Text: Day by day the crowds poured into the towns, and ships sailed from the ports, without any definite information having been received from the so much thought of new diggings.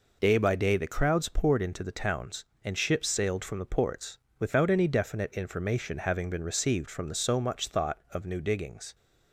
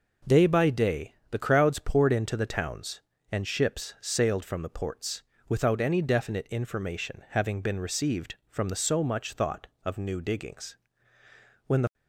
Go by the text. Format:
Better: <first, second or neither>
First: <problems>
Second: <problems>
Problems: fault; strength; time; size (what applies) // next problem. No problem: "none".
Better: first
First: none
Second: pauses between "day" and "the"; slight; at 1.1 s; 0.16 s long // goes on to say "When the"; slight; from 11.6 s on; 0.26 s long